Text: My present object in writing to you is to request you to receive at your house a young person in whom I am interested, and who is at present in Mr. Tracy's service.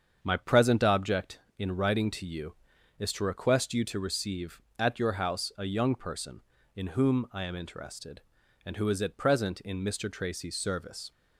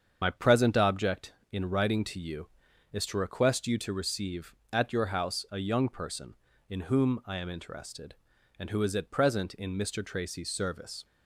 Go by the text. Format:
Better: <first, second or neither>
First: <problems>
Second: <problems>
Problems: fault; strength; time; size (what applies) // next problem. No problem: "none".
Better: first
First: starts louder than the rest; strong; until 1.2 s; 7.5 dB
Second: loses the start of "My"; at 0.2 s; 50 ms // starts louder than the rest; strong; until 1.2 s; 7.5 dB